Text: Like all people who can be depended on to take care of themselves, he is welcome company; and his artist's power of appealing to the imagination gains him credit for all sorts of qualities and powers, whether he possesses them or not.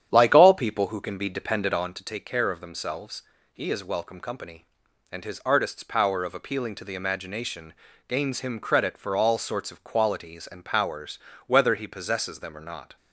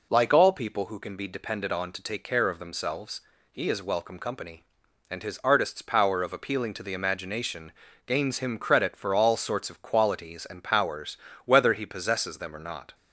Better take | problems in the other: second | starts louder than the rest; strong; until 2.0 s; 9.5 dB // pauses between "imagination" and "gains"; slight; at 7.7 s; 0.34 s long; slight in the second

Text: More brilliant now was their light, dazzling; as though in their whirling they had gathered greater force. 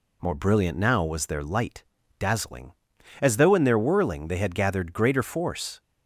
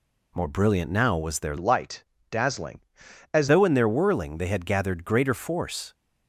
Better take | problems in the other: first | changes voice from "light" to "as"; from 1.5 to 3.4 s; 1.9 s long

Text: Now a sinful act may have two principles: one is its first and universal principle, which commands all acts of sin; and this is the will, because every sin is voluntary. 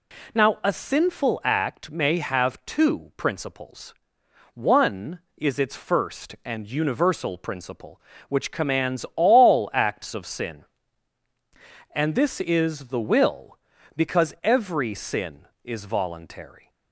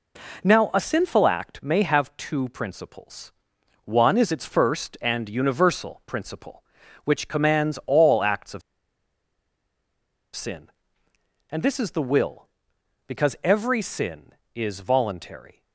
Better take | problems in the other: first | pauses between "of" and "sin"; strong; at 8.6 s; 1.7 s long

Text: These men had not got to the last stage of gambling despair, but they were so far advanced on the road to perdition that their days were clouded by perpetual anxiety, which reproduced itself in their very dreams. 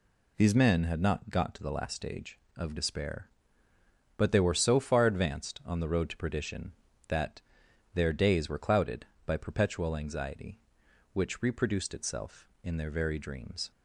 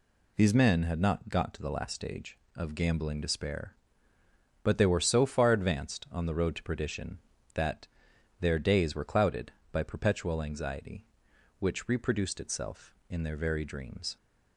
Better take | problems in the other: second | skips "gambling"; at 2.7 s // pauses between "that" and "their"; noticeable; at 7.4 s; 0.54 s long; noticeable in the second

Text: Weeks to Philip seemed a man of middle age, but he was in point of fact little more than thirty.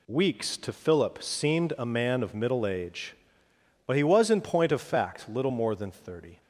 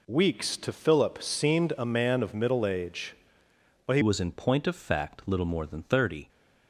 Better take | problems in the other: first | changes voice at "was"; from 4.0 s on; 2.2 s long

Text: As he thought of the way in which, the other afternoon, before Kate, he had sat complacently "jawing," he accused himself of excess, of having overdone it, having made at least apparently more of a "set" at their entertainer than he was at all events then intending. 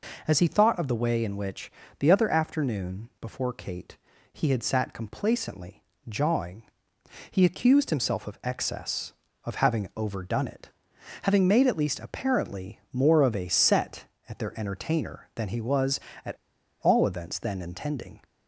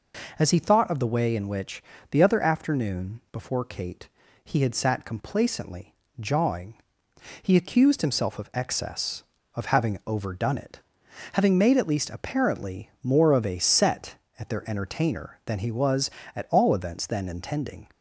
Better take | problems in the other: second | pauses between "complacently" and "jawing"; slight; at 5.8 s; 0.24 s long; slight in the second // pauses between "at" and "all"; at 16.3 s; 0.44 s long

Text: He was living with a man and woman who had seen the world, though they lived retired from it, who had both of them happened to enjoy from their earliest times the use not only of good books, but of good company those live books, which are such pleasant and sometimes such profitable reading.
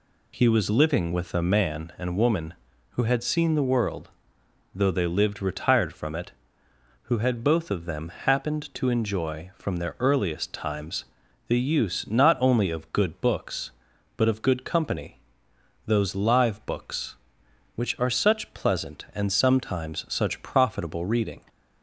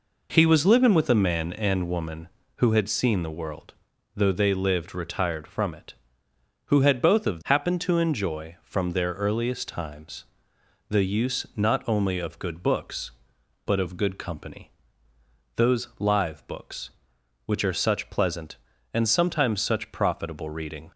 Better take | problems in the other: first | skips "them"; at 7.4 s // pauses between "times" and "the"; noticeable; at 10.2 s; 0.64 s long; also in the first // pauses between "company" and "those"; noticeable; at 14.6 s; 0.86 s long; noticeable in the first

